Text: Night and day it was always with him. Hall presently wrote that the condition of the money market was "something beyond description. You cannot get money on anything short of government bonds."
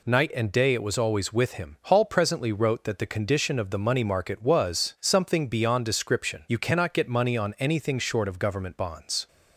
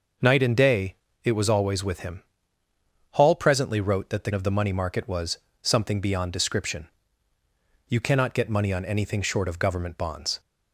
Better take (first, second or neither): first